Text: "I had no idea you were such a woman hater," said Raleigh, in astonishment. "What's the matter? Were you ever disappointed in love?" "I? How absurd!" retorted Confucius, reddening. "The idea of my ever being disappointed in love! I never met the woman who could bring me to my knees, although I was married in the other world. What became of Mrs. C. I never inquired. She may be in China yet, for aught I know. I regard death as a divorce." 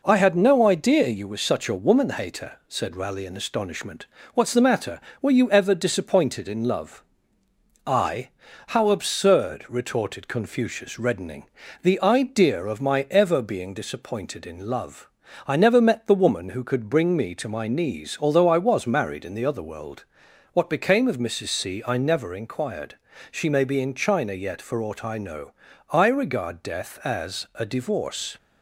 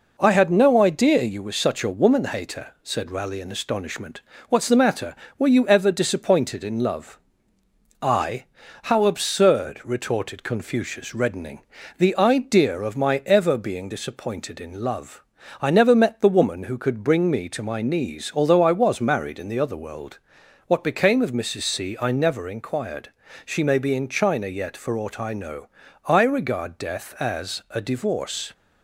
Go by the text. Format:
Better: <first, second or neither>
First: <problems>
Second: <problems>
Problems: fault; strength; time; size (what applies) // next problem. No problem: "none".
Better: neither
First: none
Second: none